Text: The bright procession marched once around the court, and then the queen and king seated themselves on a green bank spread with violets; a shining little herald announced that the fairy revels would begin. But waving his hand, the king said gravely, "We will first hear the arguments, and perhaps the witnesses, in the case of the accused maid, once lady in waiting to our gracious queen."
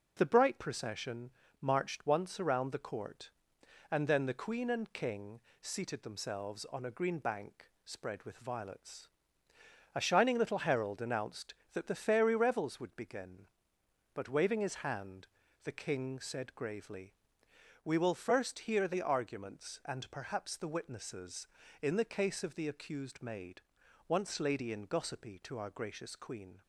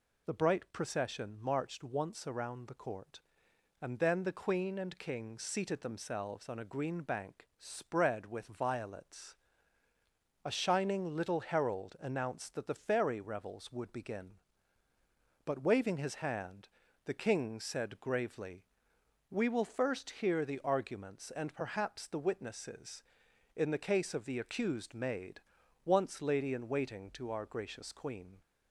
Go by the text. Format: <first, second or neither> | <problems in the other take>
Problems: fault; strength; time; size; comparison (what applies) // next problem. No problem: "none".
second | pauses between "procession" and "marched"; slight; at 1.2 s; 0.32 s long // pauses between "king" and "seated"; slight; at 5.3 s; 0.22 s long // pauses between "bank" and "spread"; slight; at 7.6 s; 0.16 s long // says "gossipy" for "waiting"; at 24.8 s